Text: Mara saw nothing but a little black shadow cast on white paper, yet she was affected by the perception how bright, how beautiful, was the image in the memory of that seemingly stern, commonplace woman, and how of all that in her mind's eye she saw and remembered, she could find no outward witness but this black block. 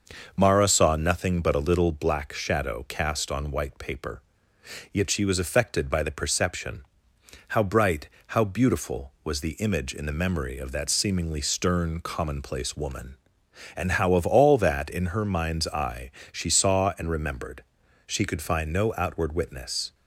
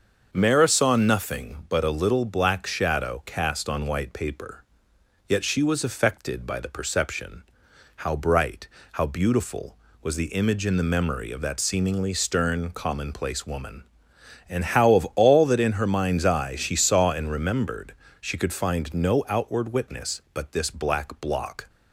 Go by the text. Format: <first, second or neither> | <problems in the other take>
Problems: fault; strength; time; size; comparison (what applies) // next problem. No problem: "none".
second | starts louder than the rest; noticeable; until 1.3 s; 6 dB; also in the second // pauses between "perception" and "how"; noticeable; at 6.8 s; 0.64 s long; noticeable in the second // pauses between "eye" and "she"; slight; at 16.1 s; 0.22 s long // stops before "but this black block"; at 19.9 s